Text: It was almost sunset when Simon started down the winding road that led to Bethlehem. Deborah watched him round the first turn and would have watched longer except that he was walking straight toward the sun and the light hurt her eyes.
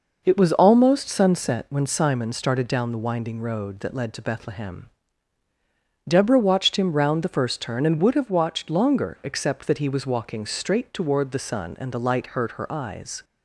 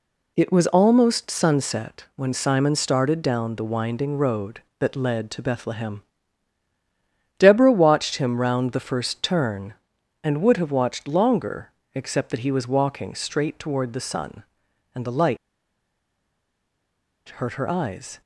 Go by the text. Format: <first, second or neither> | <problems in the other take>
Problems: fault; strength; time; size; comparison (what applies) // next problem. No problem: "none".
first | pauses between "longer" and "except"; slight; at 11.7 s; 0.24 s long // pauses between "light" and "hurt"; strong; at 15.3 s; 1.9 s long